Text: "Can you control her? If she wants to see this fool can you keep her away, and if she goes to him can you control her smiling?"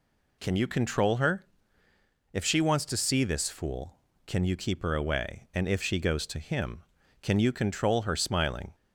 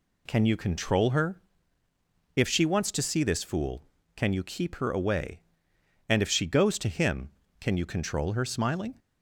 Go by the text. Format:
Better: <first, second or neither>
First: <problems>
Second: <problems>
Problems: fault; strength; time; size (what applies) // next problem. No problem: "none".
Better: neither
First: none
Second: none